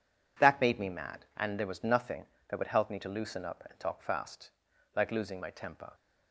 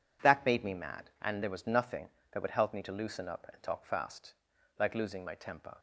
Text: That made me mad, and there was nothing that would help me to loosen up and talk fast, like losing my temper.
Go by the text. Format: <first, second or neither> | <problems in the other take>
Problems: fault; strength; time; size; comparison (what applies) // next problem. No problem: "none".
neither | none